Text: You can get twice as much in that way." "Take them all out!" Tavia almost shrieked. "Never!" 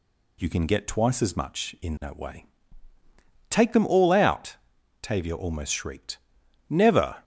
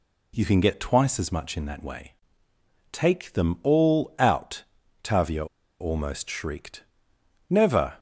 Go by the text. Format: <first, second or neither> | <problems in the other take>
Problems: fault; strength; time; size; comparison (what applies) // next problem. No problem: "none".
first | pauses between "Tavia" and "almost"; slight; at 5.4 s; 0.34 s long